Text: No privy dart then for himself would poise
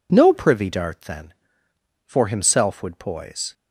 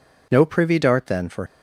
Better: first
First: none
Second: stops before "himself would poise"; at 1.4 s

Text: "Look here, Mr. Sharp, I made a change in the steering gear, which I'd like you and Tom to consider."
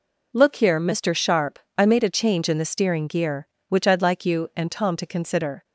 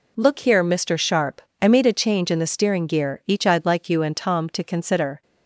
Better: first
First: none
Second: says "each" for "which"; at 3.2 s

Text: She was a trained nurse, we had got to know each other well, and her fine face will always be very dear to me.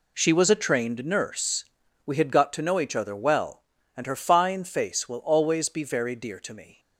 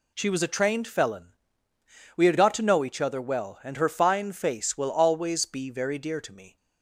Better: first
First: none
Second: says "felon" for "nurse"; at 0.8 s

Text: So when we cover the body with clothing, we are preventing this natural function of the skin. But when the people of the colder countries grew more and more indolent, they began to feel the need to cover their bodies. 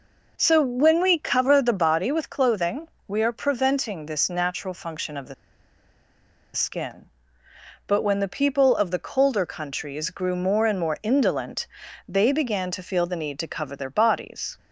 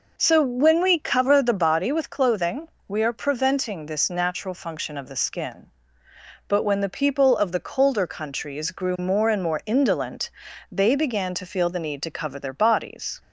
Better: second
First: pauses between "the" and "skin"; at 5.3 s; 1.2 s long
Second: none

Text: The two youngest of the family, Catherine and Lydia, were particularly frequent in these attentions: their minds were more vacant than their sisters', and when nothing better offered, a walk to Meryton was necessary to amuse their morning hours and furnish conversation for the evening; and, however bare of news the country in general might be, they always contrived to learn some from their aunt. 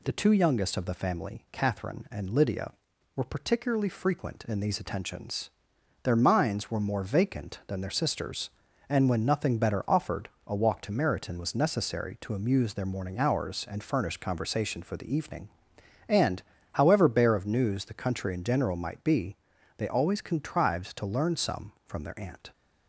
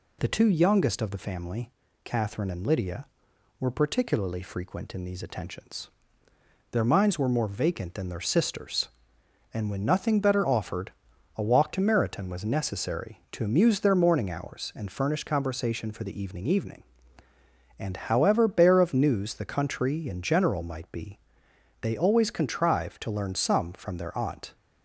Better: first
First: none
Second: says "evening" twice; at 16.4 s

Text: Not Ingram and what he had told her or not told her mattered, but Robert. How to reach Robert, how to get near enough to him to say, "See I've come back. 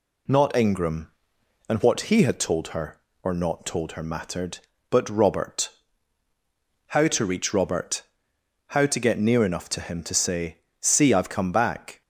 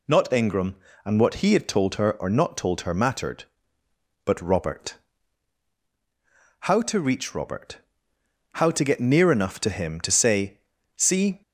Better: first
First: none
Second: stops before "I've come back"; at 11.4 s

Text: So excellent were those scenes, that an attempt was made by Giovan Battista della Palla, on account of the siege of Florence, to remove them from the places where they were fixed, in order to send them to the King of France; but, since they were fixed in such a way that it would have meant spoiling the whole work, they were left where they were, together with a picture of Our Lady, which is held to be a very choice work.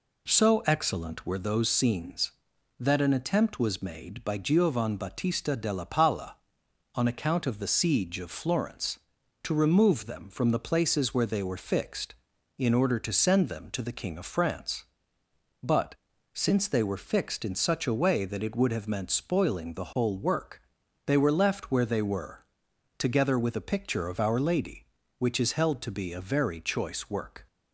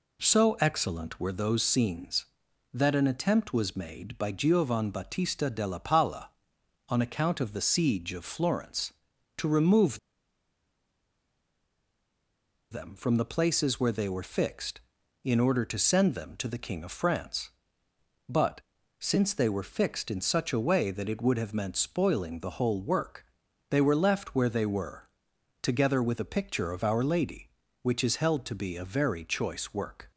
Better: first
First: none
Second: pauses between "remove" and "them"; strong; at 9.9 s; 2.7 s long

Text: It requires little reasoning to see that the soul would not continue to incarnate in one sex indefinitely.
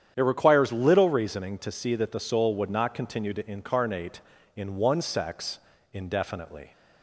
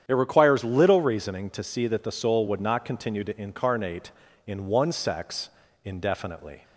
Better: neither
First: starts louder than the rest; strong; until 1.1 s; 9 dB // pauses between "sex" and "indefinitely"; slight; at 5.5 s; 0.35 s long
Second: starts louder than the rest; strong; until 1.0 s; 9 dB // pauses between "sex" and "indefinitely"; slight; at 5.4 s; 0.36 s long

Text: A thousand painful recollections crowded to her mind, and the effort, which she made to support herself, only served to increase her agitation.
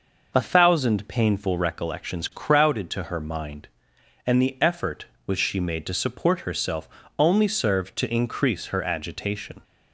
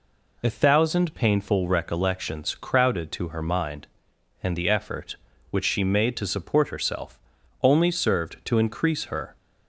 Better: first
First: none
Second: stops before "agitation"; at 9.3 s

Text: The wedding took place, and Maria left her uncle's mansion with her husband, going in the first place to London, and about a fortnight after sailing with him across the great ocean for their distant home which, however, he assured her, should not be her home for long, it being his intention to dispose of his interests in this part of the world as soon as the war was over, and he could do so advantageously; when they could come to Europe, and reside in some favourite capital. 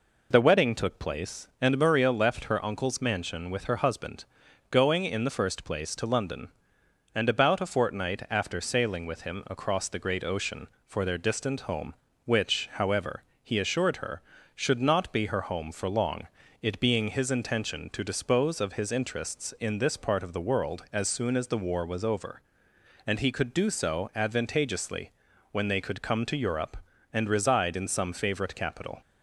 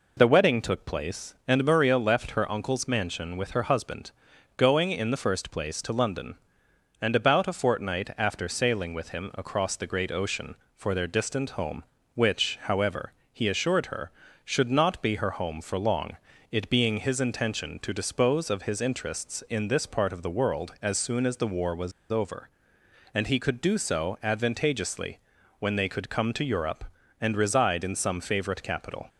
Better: first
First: none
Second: pauses between "was" and "over"; slight; at 21.9 s; 0.20 s long

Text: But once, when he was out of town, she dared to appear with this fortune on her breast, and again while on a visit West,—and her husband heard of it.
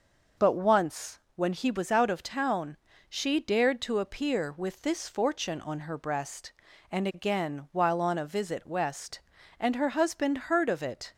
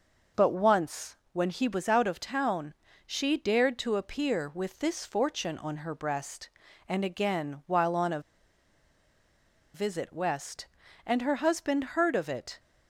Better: first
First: none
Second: pauses between "a" and "visit"; strong; at 8.1 s; 1.5 s long

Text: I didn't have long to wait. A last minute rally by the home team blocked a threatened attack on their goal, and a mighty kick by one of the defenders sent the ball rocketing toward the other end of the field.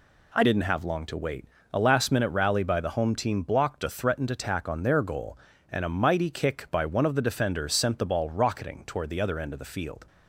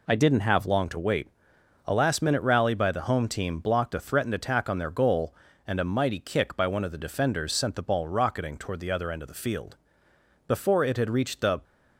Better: first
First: none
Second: goes on to say "Before it had reached the"; noticeable; from 10.4 s on; 1.1 s long

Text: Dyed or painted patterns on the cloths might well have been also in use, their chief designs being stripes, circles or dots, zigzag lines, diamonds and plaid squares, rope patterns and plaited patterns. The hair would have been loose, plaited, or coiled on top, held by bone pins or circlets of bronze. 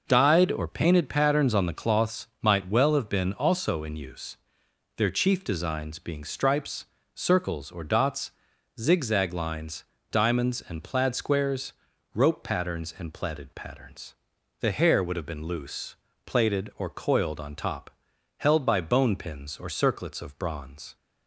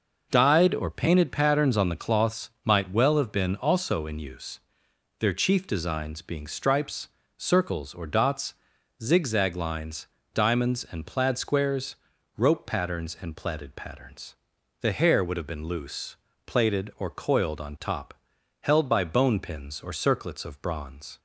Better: neither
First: none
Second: none

